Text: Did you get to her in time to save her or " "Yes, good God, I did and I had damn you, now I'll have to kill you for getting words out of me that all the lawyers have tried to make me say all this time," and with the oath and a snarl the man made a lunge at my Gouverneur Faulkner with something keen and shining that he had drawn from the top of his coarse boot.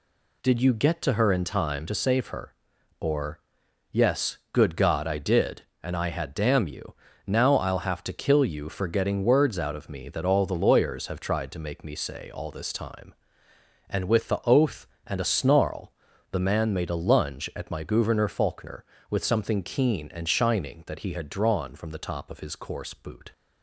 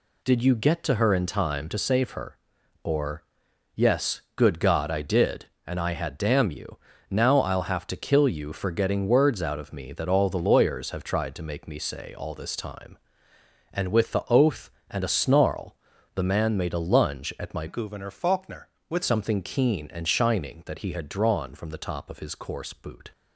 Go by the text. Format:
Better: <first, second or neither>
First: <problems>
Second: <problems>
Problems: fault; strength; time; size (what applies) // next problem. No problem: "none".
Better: first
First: pauses between "snarl" and "the"; at 15.9 s; 0.38 s long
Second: pauses between "snarl" and "the"; at 15.7 s; 0.38 s long // changes voice from "Gouverneur" to "with"; from 17.6 to 19.0 s; 1.4 s long